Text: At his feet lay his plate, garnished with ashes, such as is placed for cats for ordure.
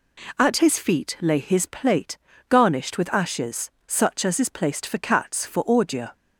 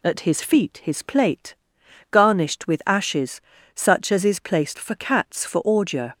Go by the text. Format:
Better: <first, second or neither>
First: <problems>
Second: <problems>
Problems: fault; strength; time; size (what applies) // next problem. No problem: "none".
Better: first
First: none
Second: skips "lay"; at 0.8 s